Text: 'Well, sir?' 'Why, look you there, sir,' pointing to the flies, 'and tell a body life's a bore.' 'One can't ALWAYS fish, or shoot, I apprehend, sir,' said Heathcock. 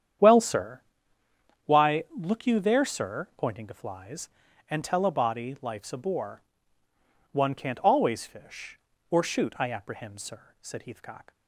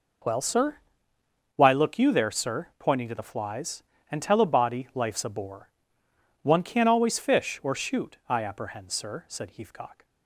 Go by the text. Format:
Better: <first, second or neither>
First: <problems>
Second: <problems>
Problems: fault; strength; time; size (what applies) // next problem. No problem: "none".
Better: second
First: starts louder than the rest; strong; until 2.0 s; 9 dB // skips "the"; at 3.7 s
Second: none